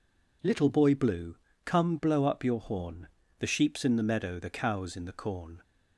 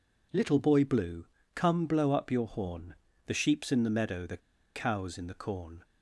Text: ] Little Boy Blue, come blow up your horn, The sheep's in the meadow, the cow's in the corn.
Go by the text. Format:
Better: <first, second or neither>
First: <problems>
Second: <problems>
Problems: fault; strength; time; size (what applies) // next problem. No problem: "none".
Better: first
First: none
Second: pauses between "the" and "cow's"; at 4.3 s; 0.37 s long